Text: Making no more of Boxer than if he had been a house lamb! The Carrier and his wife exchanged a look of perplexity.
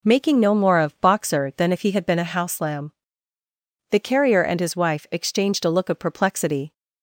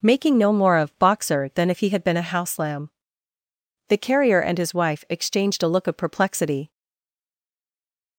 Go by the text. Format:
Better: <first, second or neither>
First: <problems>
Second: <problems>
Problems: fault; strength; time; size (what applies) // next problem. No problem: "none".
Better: first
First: none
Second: stays silent after the last word; noticeable; from 6.7 s on; 1.4 s long